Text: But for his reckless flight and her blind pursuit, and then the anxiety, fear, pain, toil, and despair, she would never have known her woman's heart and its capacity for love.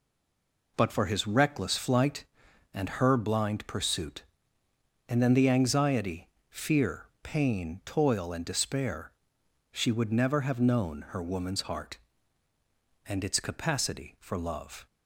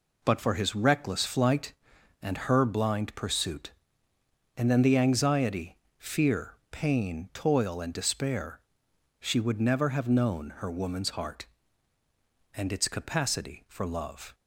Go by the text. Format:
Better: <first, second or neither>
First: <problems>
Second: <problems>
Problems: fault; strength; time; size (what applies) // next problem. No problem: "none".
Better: second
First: stays silent before the first word; slight; until 0.7 s; 0.7 s long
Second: none